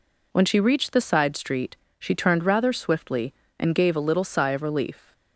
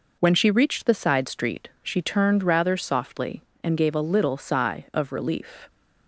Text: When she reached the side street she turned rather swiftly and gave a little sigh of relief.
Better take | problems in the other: first | pauses between "street" and "she"; slight; at 1.6 s; 0.16 s long; slight in the first // says "softly" for "swiftly"; at 2.7 s

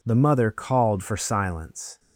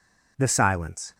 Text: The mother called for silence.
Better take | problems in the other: first | skips "mother called for"; at 0.4 s

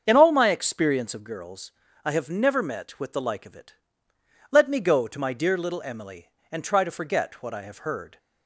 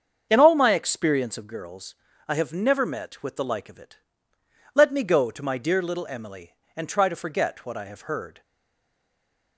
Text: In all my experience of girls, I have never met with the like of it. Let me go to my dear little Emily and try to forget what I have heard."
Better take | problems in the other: first | starts louder than the rest; until 1.3 s; 7 dB; also in the first // stays silent after the last word; noticeable; from 8.4 s on; 1.1 s long

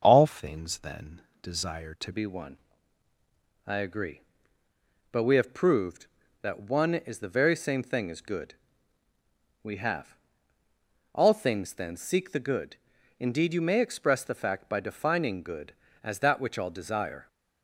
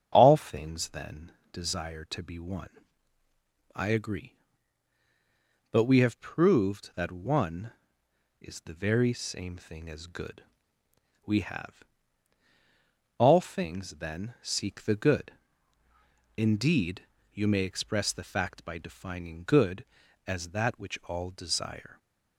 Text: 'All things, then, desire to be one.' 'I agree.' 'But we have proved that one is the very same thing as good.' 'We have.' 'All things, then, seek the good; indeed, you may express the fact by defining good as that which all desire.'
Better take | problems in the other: second | starts louder than the rest; until 1.0 s; 6.5 dB; strong in the second // changes voice at "be"; from 2.1 s on; 15.1 s long

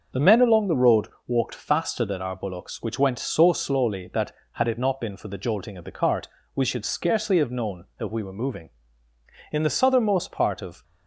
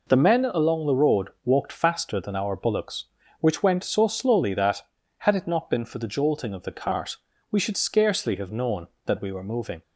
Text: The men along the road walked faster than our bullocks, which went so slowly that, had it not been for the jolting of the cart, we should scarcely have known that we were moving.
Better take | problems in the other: second | starts louder than the rest; noticeable; until 1.3 s; 6 dB // pauses between "road" and "walked"; slight; at 1.0 s; 0.20 s long // goes on to say "In the southernmost part of"; noticeable; from 9.5 s on; 1.3 s long

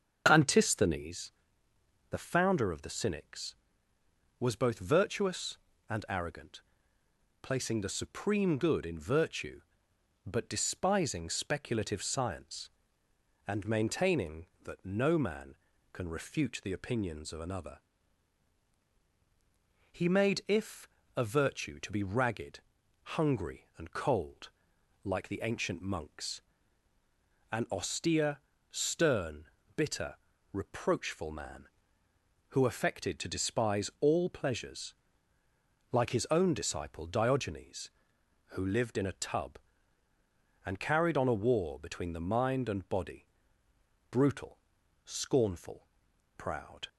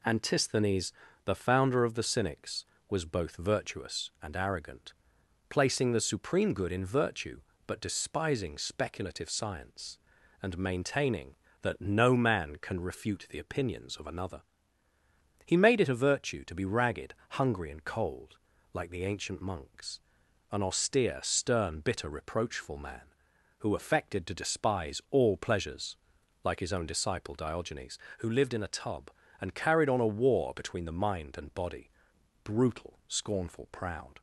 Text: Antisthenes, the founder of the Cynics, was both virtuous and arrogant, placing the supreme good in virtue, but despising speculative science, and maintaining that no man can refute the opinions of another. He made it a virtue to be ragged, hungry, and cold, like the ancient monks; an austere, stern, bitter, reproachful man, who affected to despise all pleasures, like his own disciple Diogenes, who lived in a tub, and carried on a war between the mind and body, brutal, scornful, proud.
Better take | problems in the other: second | starts louder than the rest; until 1.2 s; 6.5 dB // says "if" for "it"; at 20.4 s

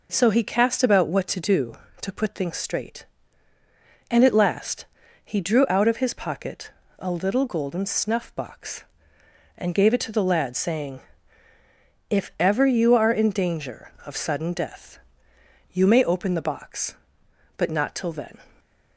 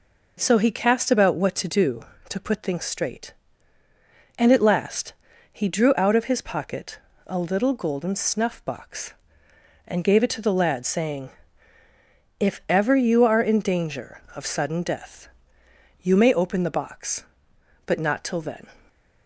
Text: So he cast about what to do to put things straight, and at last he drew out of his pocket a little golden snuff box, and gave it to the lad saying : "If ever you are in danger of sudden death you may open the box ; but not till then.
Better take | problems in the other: neither | pauses between "last" and "he"; the same in both // pauses between "pocket" and "a"; slight; the same in both // pauses between "death" and "you"; noticeable; the same in both

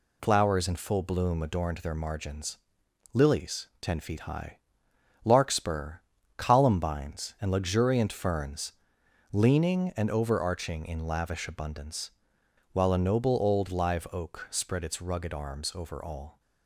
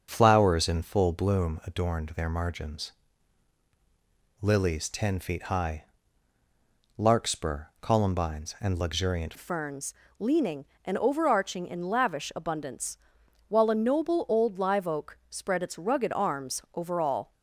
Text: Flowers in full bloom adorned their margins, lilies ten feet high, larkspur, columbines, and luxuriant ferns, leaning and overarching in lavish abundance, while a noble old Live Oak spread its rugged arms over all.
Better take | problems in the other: first | starts louder than the rest; until 1.1 s; 6.5 dB // changes voice at "ferns"; from 9.3 s on; 8.0 s long

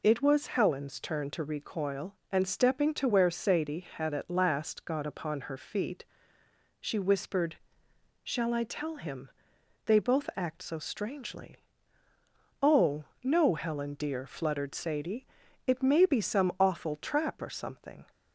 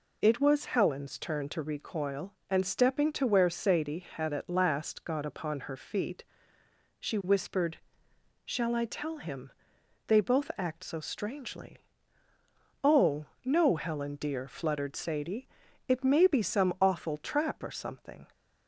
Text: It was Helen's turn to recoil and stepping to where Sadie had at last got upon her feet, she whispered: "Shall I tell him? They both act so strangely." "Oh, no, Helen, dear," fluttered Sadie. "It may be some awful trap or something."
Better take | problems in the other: neither | none

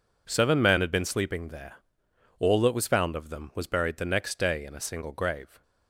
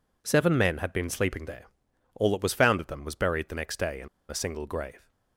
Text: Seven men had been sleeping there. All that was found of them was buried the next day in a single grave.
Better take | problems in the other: first | pauses between "in" and "a"; slight; at 4.0 s; 0.22 s long

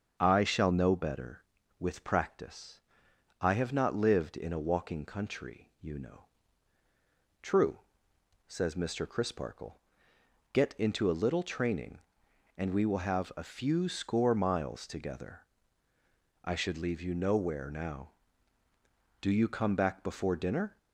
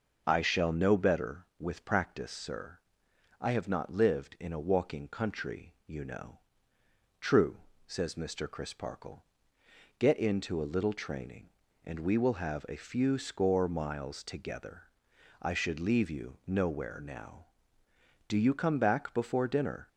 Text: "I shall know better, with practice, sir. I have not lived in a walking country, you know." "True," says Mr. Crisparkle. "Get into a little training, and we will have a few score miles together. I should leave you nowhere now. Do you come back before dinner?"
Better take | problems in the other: second | starts louder than the rest; until 1.2 s; 7 dB // skips "sir"; at 3.0 s

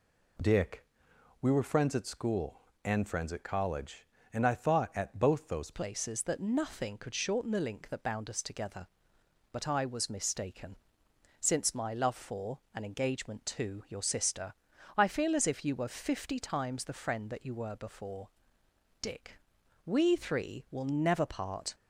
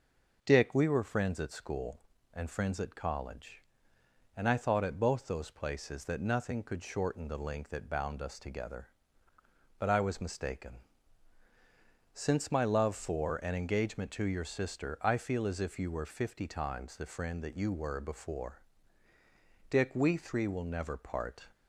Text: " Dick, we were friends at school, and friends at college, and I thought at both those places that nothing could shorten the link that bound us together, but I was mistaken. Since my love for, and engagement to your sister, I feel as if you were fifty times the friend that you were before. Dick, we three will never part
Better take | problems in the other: second | changes voice at "places"; from 5.7 s on; 16.0 s long

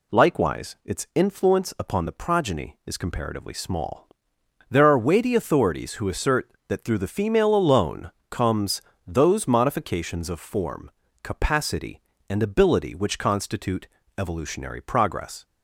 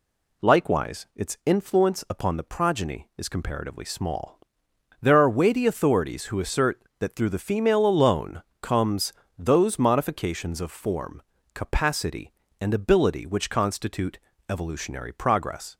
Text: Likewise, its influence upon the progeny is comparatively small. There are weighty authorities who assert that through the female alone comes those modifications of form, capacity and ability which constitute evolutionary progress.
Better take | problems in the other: neither | pauses between "alone" and "comes"; slight; the same in both // pauses between "comes" and "those"; slight; the same in both // pauses between "constitute" and "evolutionary"; slight; the same in both

